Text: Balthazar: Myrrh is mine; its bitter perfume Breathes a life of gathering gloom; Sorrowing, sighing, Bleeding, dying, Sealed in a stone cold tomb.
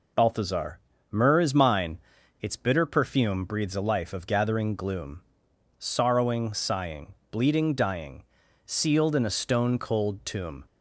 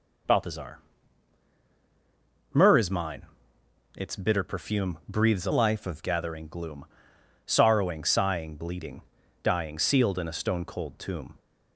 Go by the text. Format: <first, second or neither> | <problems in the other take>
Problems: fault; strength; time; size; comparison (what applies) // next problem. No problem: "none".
first | changes voice from "life" to "of"; from 5.5 to 6.0 s; 0.5 s long